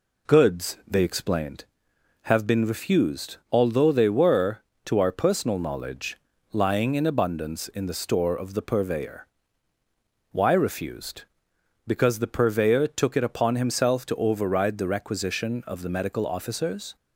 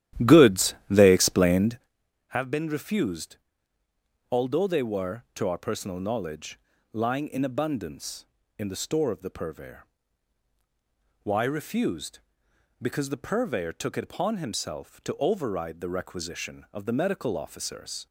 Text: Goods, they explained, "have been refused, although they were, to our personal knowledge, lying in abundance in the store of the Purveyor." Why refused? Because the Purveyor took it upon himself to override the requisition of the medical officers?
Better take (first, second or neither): first